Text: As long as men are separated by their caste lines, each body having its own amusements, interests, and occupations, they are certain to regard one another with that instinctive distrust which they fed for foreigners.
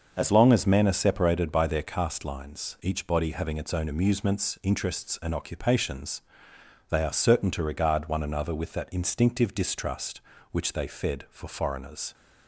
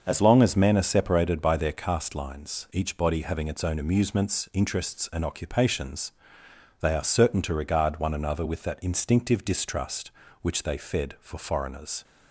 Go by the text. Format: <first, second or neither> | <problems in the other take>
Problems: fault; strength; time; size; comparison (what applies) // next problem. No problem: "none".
neither | starts louder than the rest; the same in both